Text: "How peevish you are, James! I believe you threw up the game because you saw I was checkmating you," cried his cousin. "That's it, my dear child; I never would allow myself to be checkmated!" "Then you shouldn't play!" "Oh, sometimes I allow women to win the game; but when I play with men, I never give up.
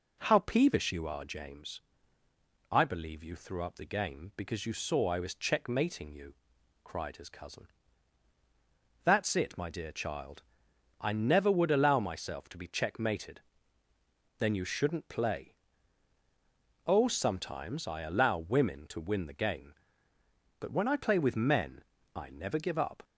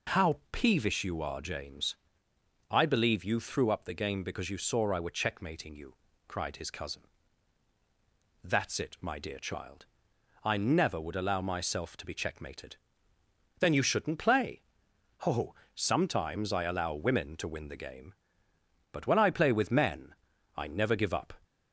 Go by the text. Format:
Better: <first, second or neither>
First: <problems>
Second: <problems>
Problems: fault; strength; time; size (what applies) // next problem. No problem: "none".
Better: first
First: none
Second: says "were" for "was"; at 4.9 s